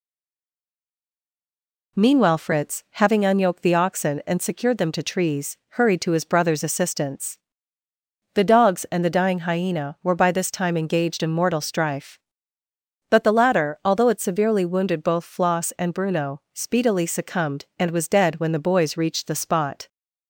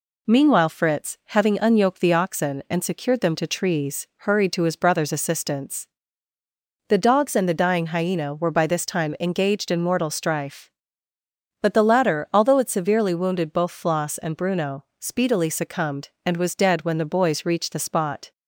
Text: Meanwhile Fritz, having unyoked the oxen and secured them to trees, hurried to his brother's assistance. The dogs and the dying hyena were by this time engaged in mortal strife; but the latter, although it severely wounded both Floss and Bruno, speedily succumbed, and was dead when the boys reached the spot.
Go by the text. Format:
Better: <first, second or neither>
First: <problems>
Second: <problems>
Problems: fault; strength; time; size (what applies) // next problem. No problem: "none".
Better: second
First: stays silent before the first word; noticeable; until 1.9 s; 1.9 s long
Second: none